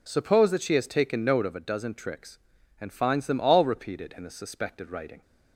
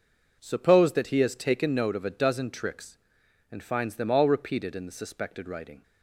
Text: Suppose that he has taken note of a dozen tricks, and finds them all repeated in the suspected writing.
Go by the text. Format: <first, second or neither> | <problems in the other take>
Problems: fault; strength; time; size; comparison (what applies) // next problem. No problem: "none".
second | says "she" for "he"; at 0.6 s